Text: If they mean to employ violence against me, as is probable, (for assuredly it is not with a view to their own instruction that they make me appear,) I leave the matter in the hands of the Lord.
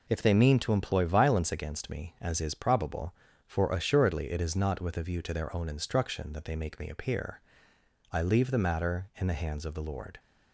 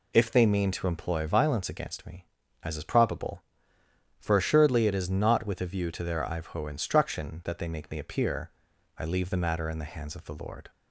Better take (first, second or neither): first